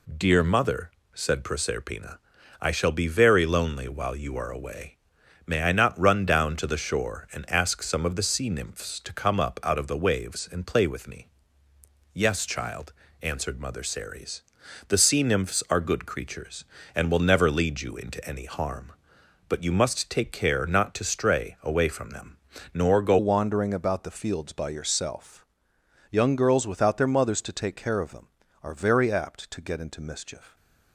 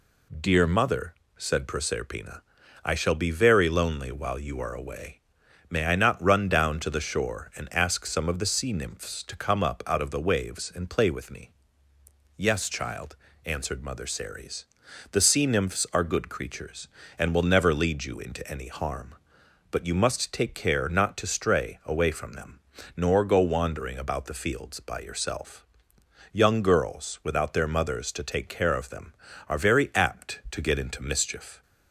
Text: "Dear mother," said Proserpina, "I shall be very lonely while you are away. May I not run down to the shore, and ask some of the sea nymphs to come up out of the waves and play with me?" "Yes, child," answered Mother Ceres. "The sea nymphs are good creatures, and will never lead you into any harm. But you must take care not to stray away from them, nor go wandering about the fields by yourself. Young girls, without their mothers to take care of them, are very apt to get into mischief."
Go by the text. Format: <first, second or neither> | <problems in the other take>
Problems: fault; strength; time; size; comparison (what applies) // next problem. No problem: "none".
second | changes voice at "wandering"; from 23.1 s on; 7.4 s long